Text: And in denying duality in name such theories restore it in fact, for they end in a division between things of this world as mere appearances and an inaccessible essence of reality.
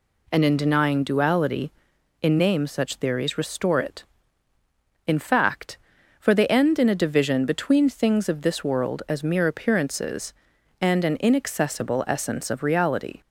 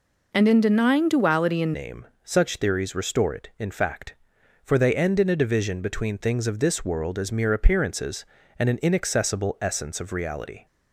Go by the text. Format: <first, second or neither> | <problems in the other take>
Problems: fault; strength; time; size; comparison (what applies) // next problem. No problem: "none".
first | changes voice at "name"; from 1.7 s on; 8.9 s long // pauses between "name" and "such"; slight; at 2.0 s; 0.20 s long